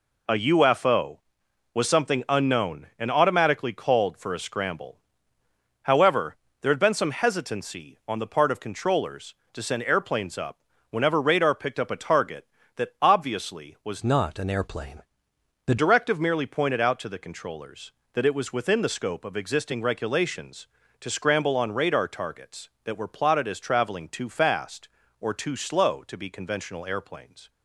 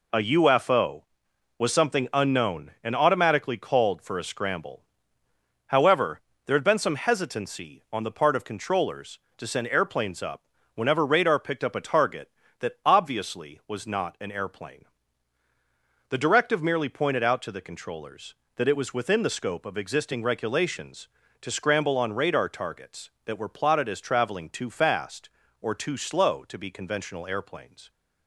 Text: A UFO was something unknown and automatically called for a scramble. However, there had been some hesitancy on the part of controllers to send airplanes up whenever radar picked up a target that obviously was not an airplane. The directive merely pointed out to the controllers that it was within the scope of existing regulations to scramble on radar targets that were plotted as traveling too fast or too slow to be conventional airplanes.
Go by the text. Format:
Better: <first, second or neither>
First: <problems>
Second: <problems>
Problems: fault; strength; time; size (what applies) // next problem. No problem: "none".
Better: second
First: pauses between "up" and "whenever"; slight; at 10.5 s; 0.32 s long // changes voice from "not" to "The"; from 14.0 to 15.7 s; 1.7 s long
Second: pauses between "up" and "whenever"; slight; at 10.4 s; 0.32 s long